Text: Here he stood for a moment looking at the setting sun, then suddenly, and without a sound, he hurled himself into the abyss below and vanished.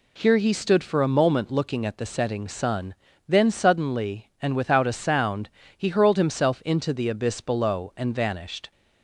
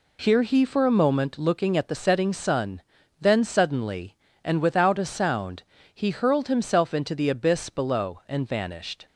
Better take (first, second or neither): first